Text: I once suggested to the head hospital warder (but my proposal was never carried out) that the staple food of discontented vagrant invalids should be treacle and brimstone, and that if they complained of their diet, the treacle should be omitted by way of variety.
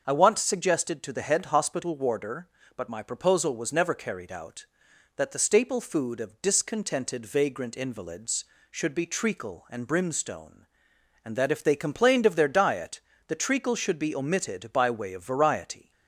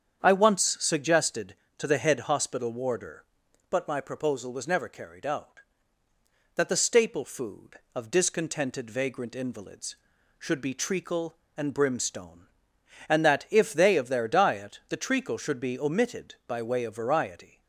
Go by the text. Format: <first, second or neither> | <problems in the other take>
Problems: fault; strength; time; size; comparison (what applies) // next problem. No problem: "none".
first | starts louder than the rest; strong; until 1.2 s; 8 dB; also in the first // skips "complained"; at 13.9 s